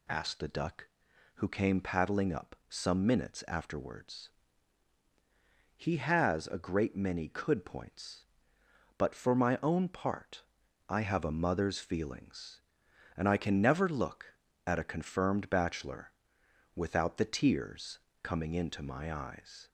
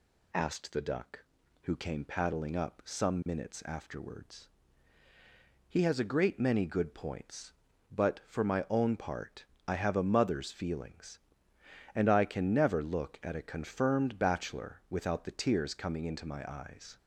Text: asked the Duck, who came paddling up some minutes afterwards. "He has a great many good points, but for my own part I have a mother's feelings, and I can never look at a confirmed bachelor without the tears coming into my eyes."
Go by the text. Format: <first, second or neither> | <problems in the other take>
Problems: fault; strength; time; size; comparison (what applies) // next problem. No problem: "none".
second | says "could" for "good"; at 7.2 s // pauses between "part" and "I"; noticeable; at 10.4 s; 0.48 s long; slight in the second // pauses between "bachelor" and "without"; noticeable; at 16.1 s; 0.64 s long // pauses between "tears" and "coming"; slight; at 17.9 s; 0.24 s long